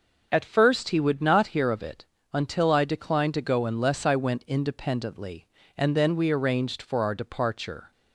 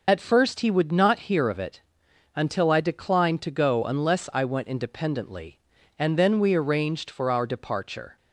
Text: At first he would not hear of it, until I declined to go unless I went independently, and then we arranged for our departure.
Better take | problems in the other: first | loses the start of "At"; at 0.0 s; 35 ms

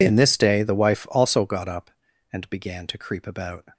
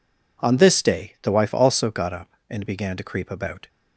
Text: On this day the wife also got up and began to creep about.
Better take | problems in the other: second | says "In" for "On"; at 0.0 s

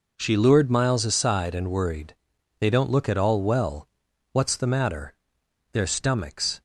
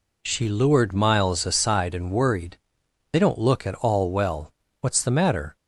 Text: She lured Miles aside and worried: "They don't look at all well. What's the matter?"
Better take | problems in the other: second | goes on to say "Their stomachs"; noticeable; from 5.7 s on; 0.88 s long

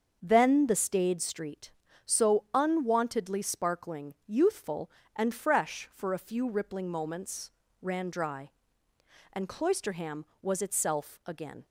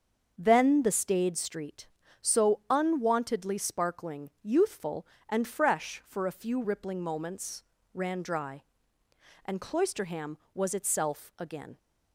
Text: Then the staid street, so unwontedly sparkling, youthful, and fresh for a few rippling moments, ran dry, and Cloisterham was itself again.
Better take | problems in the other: neither | starts louder than the rest; the same in both

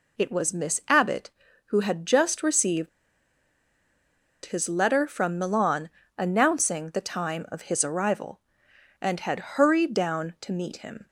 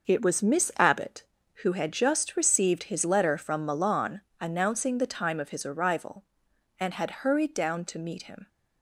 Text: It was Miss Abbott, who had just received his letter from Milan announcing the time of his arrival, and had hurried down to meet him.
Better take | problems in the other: second | pauses between "received" and "his"; strong; at 2.8 s; 1.5 s long // pauses between "Milan" and "announcing"; slight; at 5.8 s; 0.28 s long; slight in the second

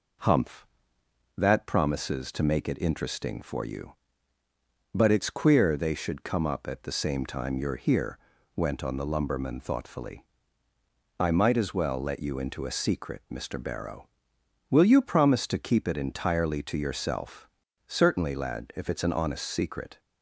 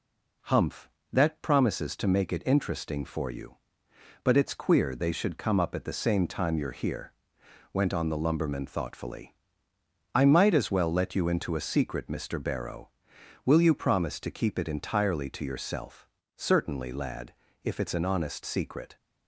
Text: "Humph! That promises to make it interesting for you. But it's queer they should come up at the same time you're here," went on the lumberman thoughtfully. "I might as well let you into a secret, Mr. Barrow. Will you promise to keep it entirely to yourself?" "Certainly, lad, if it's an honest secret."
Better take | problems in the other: neither | none

